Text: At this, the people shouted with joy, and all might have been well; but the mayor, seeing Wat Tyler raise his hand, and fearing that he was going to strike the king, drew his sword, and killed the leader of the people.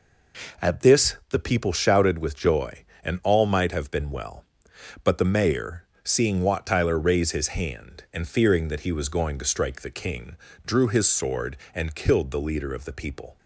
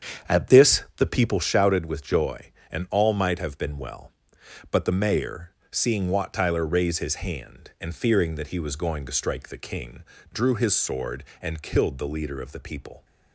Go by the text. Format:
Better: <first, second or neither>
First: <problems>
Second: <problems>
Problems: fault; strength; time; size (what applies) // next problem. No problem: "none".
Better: first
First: none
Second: starts louder than the rest; strong; until 1.6 s; 8 dB